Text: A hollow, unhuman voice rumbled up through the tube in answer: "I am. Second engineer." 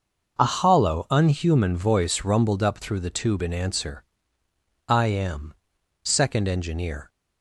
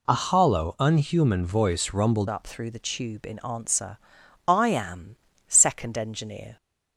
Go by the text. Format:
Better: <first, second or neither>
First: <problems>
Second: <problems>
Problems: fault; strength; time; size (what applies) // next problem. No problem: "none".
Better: first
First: none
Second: changes voice at "up"; from 2.3 s on; 4.2 s long